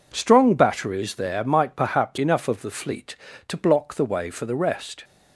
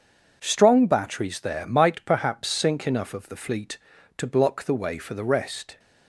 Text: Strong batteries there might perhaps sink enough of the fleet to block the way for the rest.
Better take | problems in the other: second | skips "sink"; at 2.1 s

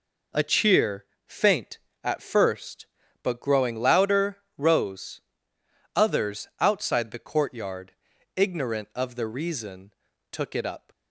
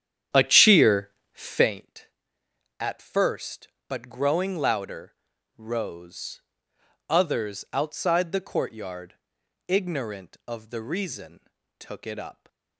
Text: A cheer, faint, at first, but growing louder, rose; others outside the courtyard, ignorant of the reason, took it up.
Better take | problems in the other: first | starts louder than the rest; strong; until 1.7 s; 9 dB

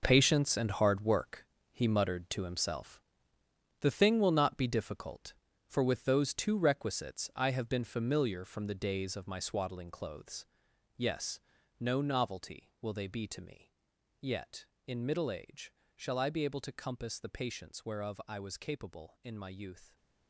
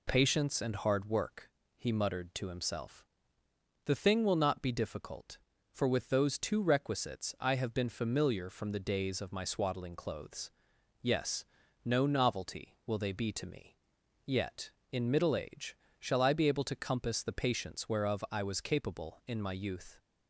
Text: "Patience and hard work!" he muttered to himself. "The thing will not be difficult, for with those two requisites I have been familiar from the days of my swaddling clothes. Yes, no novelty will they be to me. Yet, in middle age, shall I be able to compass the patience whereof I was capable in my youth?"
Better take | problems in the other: second | gets quieter; strong; throughout; 11.5 dB

